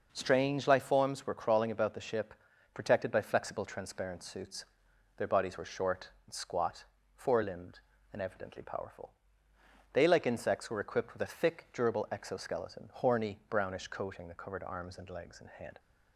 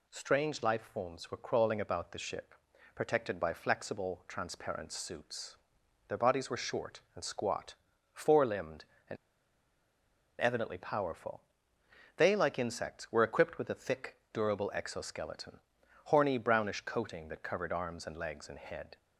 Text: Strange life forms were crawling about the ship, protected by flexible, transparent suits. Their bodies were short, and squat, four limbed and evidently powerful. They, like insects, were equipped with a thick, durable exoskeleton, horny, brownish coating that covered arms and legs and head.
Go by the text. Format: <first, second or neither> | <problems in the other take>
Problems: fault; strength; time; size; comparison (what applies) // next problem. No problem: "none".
first | pauses between "and" and "evidently"; strong; at 9.1 s; 1.2 s long